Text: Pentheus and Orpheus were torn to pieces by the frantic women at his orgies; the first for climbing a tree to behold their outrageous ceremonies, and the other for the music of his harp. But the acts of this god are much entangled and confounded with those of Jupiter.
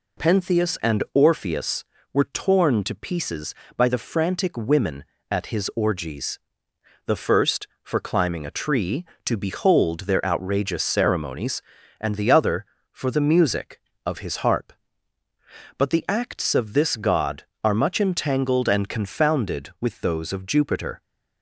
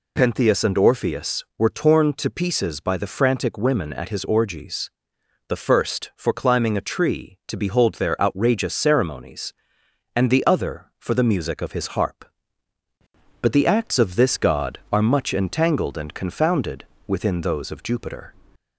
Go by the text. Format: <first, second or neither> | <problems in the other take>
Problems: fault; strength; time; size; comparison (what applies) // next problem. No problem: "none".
first | says "within" for "with"; at 17.0 s